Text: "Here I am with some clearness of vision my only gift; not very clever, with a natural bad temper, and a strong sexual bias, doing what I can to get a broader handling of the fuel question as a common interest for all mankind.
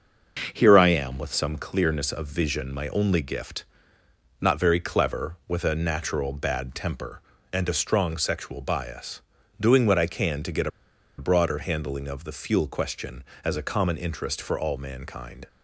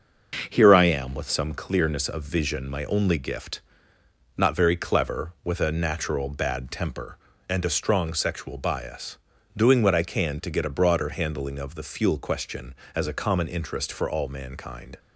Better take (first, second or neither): second